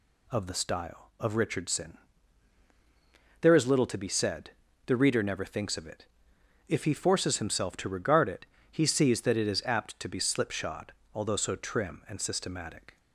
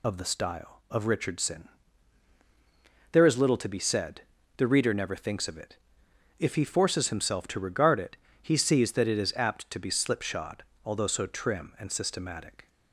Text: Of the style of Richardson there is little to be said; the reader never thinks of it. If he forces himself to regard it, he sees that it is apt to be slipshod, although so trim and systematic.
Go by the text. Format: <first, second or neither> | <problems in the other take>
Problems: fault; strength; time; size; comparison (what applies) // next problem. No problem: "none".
first | loses the start of "Of"; at 0.0 s; 45 ms // pauses between "Richardson" and "there"; strong; at 1.6 s; 1.4 s long; strong in the first